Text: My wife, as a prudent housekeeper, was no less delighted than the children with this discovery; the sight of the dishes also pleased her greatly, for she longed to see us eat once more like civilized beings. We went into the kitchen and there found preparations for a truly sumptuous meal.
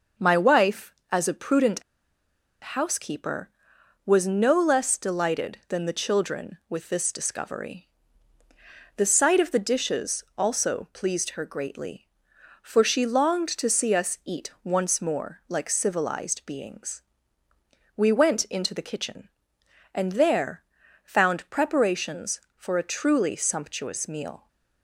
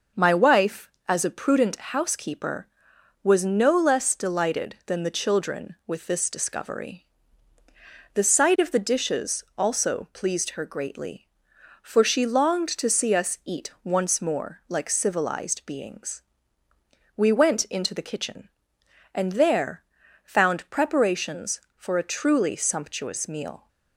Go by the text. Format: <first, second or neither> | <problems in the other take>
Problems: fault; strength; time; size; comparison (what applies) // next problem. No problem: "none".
second | pauses between "prudent" and "housekeeper"; noticeable; at 1.8 s; 0.81 s long // pauses between "there" and "found"; at 20.6 s; 0.42 s long; also in the second